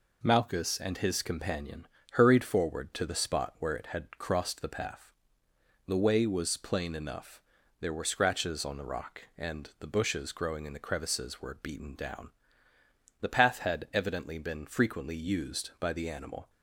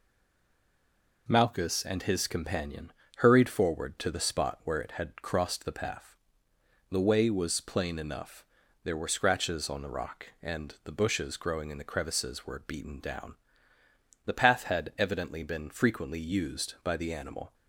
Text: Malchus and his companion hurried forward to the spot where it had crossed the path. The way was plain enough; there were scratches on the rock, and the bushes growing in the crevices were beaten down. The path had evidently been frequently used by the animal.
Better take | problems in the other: first | stays silent before the first word; noticeable; until 1.2 s; 1.2 s long // pauses between "companion" and "hurried"; slight; at 2.9 s; 0.24 s long; slight in the first

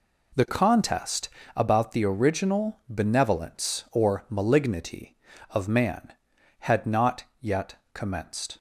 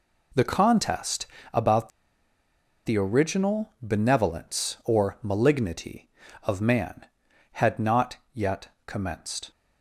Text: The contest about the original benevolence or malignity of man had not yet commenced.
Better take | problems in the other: first | pauses between "contest" and "about"; slight; at 1.2 s; 0.26 s long; slight in the first // pauses between "about" and "the"; noticeable; at 1.8 s; 0.97 s long // pauses between "not" and "yet"; slight; at 8.1 s; 0.16 s long; slight in the first // pauses between "yet" and "commenced"; slight; at 8.6 s; 0.18 s long; slight in the first

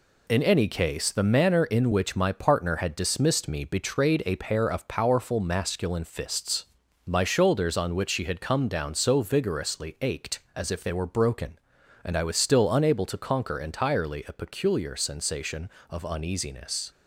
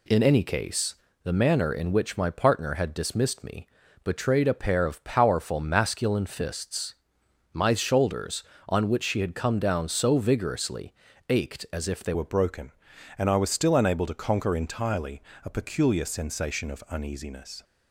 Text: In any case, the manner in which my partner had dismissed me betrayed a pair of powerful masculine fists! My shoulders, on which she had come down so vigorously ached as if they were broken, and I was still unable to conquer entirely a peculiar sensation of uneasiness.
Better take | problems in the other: first | pauses between "me" and "betrayed"; at 3.6 s; 0.38 s long // pauses between "vigorously" and "ached"; slight; at 10.9 s; 0.36 s long // changes voice at "were"; from 12.1 s on; 5.5 s long // pauses between "entirely" and "a"; slight; at 15.2 s; 0.24 s long

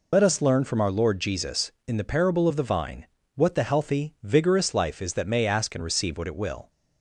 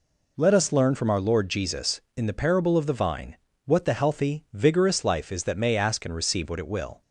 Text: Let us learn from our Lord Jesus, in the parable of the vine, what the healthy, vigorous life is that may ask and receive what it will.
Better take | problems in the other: second | loses the start of "Let"; at 0.1 s; 65 ms

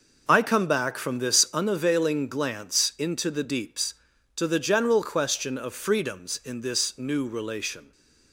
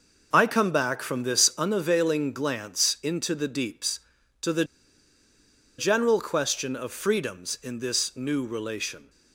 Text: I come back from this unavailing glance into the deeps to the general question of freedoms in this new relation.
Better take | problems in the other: first | pauses between "the" and "general"; at 4.6 s; 1.1 s long

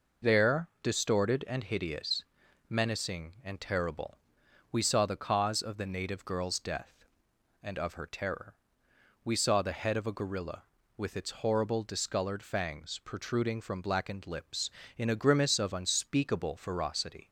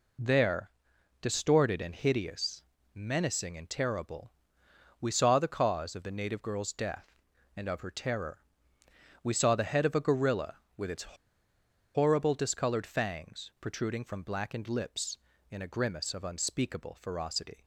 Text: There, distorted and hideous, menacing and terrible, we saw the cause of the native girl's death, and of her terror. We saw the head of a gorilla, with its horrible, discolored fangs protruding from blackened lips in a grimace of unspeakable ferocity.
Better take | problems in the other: first | pauses between "its" and "horrible"; noticeable; at 11.1 s; 0.78 s long

